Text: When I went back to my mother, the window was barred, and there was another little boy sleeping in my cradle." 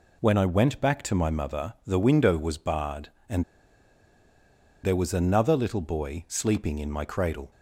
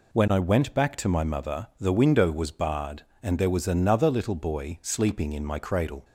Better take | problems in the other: second | pauses between "and" and "there"; strong; at 3.4 s; 1.4 s long

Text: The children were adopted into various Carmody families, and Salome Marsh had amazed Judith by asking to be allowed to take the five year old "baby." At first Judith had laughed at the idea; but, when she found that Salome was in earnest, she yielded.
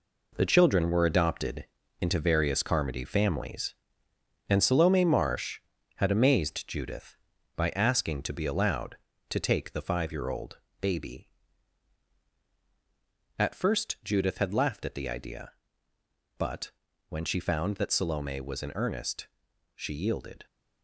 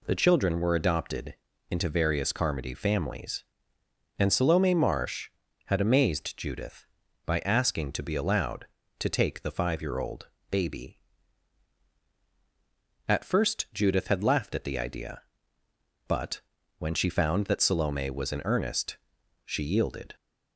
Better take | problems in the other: second | gets quieter; strong; throughout; 8 dB // pauses between "adopted" and "into"; slight; at 1.6 s; 0.34 s long; slight in the second // pauses between "old" and "baby"; slight; at 10.5 s; 0.22 s long; slight in the second

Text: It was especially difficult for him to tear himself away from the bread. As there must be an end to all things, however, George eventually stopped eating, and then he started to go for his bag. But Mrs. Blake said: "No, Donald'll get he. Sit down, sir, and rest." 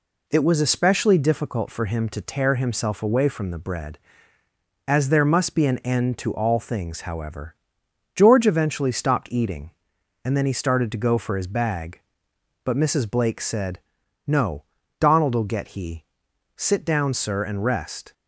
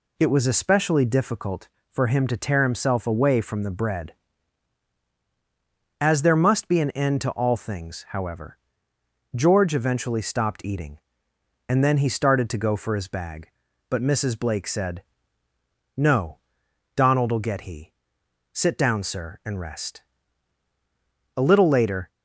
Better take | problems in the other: first | goes on to say "A little later"; noticeable; from 21.3 s on; 0.72 s long

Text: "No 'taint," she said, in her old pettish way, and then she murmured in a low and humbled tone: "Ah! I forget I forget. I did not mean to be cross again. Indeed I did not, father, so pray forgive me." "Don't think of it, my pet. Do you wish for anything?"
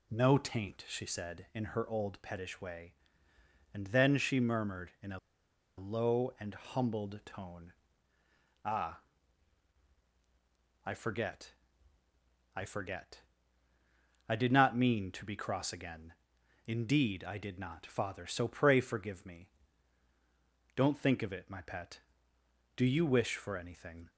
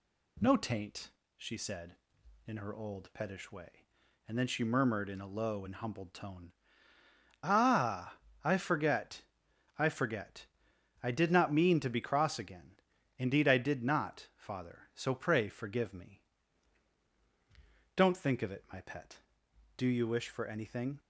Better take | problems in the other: second | pauses between "a" and "low"; noticeable; at 5.1 s; 0.58 s long // pauses between "forget" and "I"; at 11.5 s; 1.0 s long; noticeable in the second

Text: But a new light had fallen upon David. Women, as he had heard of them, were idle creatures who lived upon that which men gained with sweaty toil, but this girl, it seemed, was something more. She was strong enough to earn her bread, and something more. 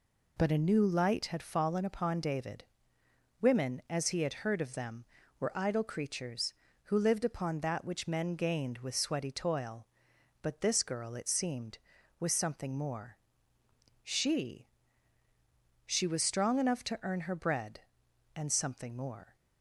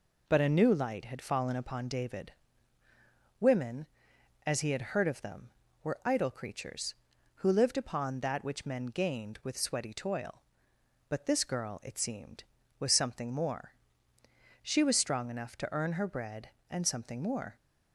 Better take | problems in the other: second | says "She" twice; at 15.8 s

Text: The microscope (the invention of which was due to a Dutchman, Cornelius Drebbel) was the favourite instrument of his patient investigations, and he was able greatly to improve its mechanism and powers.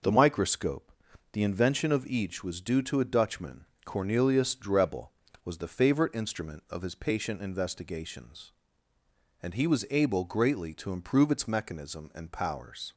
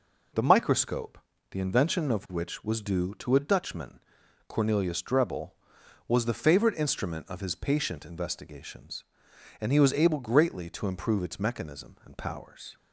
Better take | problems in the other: second | says "each" for "which"; at 2.0 s

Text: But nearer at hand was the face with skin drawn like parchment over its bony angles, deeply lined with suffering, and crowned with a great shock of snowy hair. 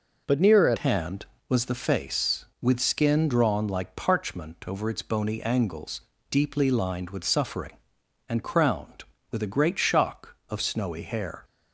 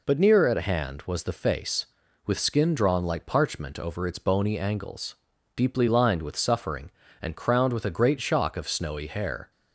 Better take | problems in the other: second | changes voice at "hand"; from 0.7 s on; 10.7 s long

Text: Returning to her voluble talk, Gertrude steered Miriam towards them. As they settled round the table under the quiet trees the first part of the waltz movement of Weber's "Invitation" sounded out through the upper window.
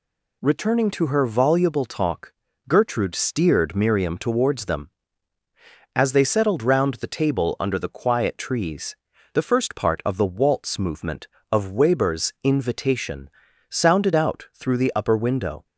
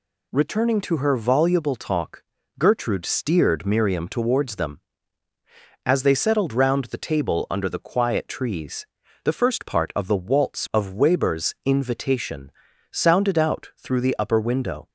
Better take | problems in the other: first | pauses between "trees" and "the"; slight; at 8.8 s; 0.36 s long; slight in the first // skips "movement"; at 10.7 s // pauses between "Invitation" and "sounded"; at 12.5 s; 0.40 s long; also in the first

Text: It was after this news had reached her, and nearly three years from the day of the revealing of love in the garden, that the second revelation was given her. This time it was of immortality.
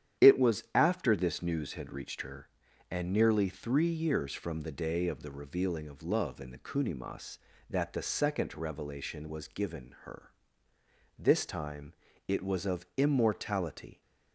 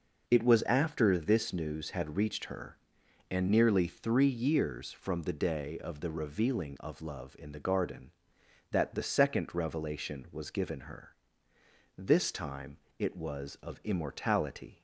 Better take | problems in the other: second | starts louder than the rest; strong; until 1.3 s; 10 dB // says "kunimas" for "garden"; at 6.5 s // pauses between "time" and "it"; slight; at 11.9 s; 0.34 s long; slight in the second

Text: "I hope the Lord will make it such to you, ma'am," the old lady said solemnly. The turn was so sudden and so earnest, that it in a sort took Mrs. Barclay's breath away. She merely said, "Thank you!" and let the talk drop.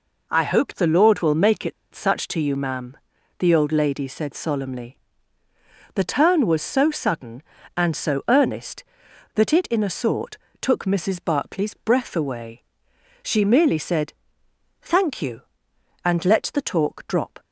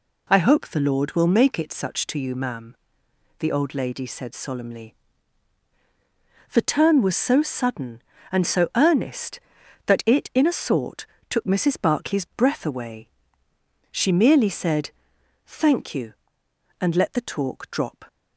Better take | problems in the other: second | pauses between "it" and "such"; slight; at 1.7 s; 0.21 s long // pauses between "sort" and "took"; slight; at 10.3 s; 0.24 s long; slight in the second

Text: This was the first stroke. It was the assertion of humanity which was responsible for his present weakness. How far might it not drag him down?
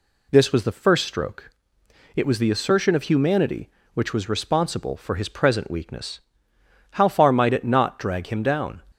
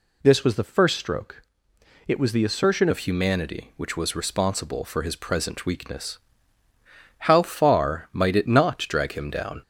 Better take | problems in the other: first | changes voice at "of"; from 2.9 s on; 6.7 s long

